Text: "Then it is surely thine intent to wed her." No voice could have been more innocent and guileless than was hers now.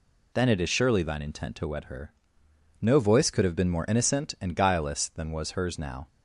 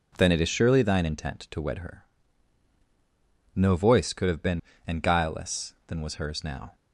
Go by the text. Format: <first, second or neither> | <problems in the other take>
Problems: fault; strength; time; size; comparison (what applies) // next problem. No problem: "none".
first | skips "more innocent"; at 4.7 s